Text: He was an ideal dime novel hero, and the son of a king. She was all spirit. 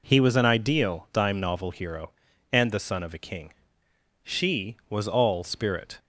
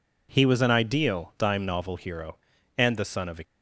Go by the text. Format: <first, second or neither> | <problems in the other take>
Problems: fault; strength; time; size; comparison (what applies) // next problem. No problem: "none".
first | stops before "king She was all spirit"; at 3.4 s